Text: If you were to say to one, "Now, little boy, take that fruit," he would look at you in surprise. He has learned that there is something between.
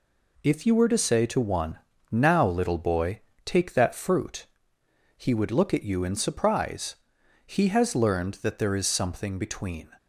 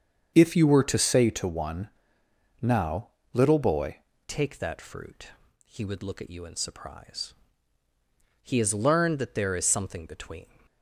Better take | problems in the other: first | starts louder than the rest; strong; until 1.3 s; 7 dB // changes voice at "take"; from 4.2 s on; 6.2 s long

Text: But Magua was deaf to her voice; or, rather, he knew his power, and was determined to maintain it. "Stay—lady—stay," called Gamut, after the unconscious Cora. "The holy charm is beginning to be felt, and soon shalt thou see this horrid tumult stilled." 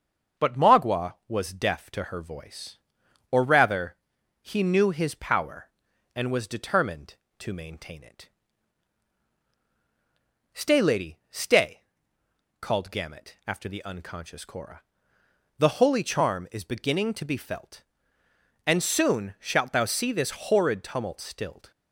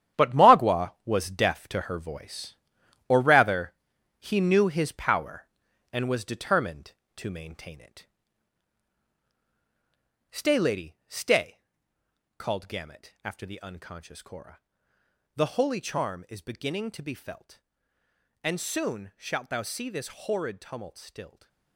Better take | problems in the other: first | gets quieter; strong; throughout; 10 dB // starts louder than the rest; strong; until 1.2 s; 10 dB; also in the first

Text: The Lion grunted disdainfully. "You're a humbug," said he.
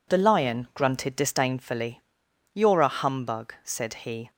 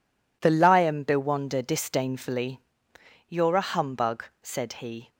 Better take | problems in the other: first | says "bewonder" for "grunted"; at 1.0 s

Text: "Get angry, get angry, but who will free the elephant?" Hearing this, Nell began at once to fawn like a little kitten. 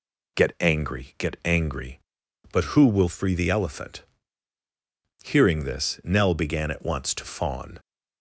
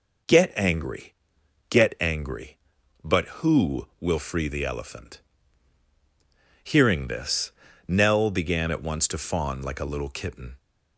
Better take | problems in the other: second | stops before "like a little kitten"; at 7.7 s

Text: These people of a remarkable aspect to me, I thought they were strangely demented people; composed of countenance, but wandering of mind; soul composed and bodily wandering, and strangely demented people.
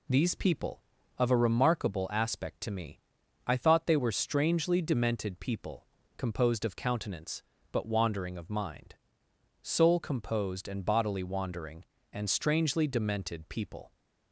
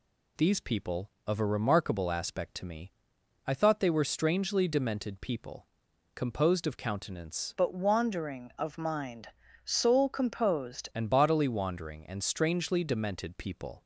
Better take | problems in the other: first | changes voice from "but" to "composed"; from 7.5 to 10.8 s; 3.3 s long

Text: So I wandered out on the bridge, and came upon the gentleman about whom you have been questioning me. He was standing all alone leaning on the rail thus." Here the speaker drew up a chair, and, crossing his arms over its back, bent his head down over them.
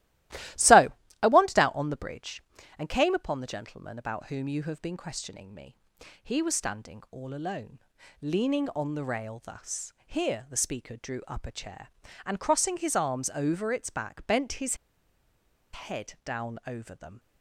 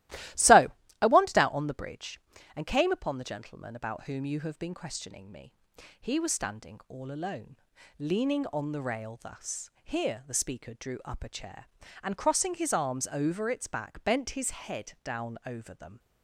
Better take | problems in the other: second | starts louder than the rest; strong; until 1.9 s; 16 dB; strong in the second // pauses between "So" and "I"; slight; at 0.8 s; 0.32 s long; slight in the second // pauses between "alone" and "leaning"; at 7.7 s; 0.42 s long; also in the second // pauses between "his" and "head"; noticeable; at 14.7 s; 0.97 s long

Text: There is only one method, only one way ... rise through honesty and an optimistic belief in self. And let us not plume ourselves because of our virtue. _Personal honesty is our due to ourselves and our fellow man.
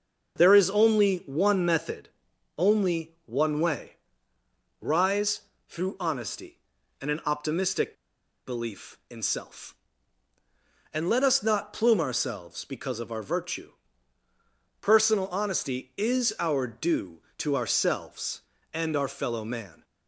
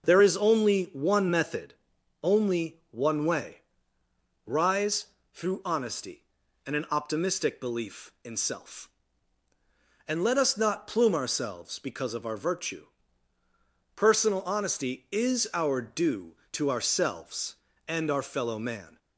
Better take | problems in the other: second | pauses between "rise" and "through"; slight; at 5.4 s; 0.26 s long; slight in the second // pauses between "optimistic" and "belief"; noticeable; at 7.9 s; 0.51 s long

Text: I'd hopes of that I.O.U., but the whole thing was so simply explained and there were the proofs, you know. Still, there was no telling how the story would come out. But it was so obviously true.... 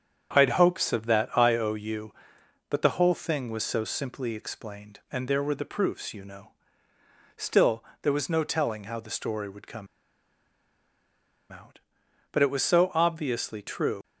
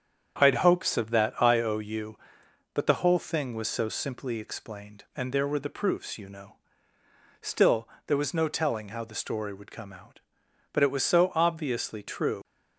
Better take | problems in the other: second | starts louder than the rest; strong; until 1.4 s; 8.5 dB; strong in the second // pauses between "come" and "out"; strong; at 9.8 s; 1.6 s long

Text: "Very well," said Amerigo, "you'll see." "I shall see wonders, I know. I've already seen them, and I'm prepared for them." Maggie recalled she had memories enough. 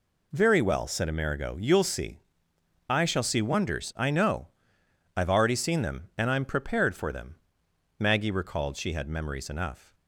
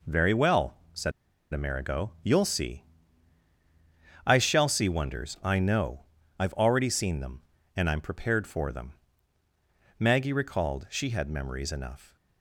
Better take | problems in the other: first | pauses between "said" and "Amerigo"; at 1.1 s; 0.41 s long

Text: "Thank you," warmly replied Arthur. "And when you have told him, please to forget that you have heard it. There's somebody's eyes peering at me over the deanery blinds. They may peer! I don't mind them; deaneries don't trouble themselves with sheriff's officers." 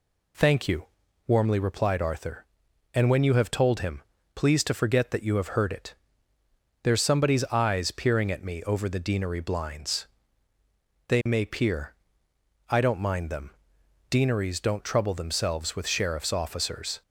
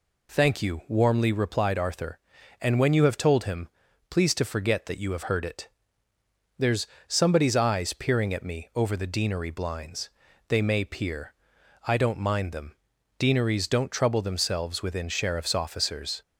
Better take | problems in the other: first | pauses between "There's" and "somebody's"; slight; at 6.8 s; 0.20 s long // says "within" for "with"; at 14.8 s

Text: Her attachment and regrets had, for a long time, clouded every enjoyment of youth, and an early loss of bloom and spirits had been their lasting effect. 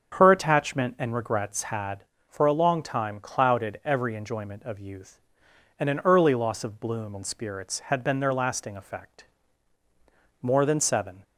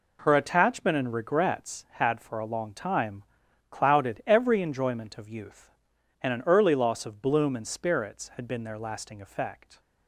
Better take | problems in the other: second | starts louder than the rest; strong; until 1.2 s; 7.5 dB // goes on to say "More than seven"; noticeable; from 10.4 s on; 0.80 s long

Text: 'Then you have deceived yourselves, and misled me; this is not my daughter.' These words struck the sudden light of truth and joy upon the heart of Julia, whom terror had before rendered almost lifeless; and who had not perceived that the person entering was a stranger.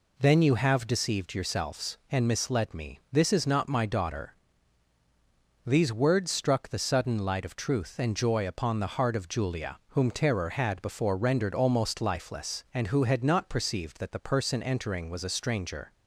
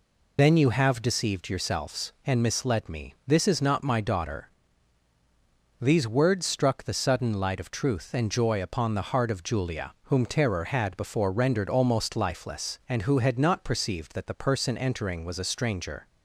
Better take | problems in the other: first | loses the start of "Then"; at 0.3 s; 55 ms

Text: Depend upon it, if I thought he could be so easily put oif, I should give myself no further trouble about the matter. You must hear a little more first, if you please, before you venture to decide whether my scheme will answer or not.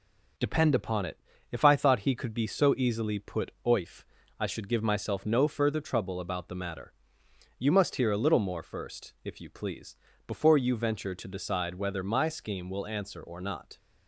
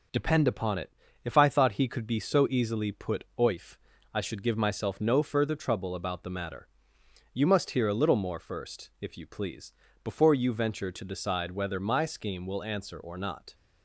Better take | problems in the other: neither | none

